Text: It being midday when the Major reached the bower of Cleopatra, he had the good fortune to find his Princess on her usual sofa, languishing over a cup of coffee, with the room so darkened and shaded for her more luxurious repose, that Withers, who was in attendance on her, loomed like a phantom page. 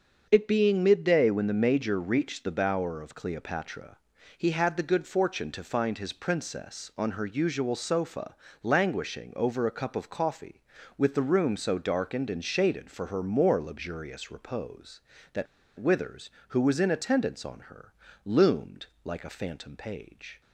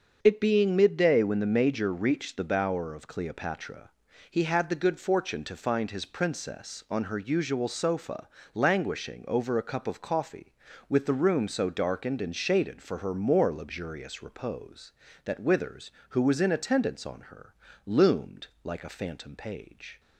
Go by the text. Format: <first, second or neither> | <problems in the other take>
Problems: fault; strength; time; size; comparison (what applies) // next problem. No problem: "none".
second | starts louder than the rest; until 1.3 s; 6.5 dB; also in the second // pauses between "that" and "Withers"; slight; at 15.4 s; 0.32 s long // pauses between "loomed" and "like"; slight; at 18.8 s; 0.18 s long; slight in the second